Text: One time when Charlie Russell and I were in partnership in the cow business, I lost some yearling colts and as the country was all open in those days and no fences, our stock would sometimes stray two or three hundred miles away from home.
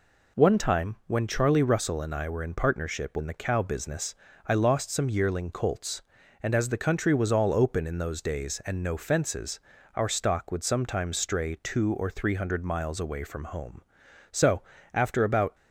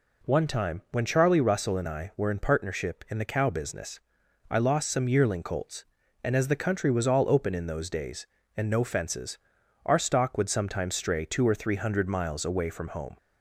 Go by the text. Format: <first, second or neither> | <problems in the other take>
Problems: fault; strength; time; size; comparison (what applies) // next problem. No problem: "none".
second | goes on to say "So after about"; noticeable; from 14.3 s on; 1.2 s long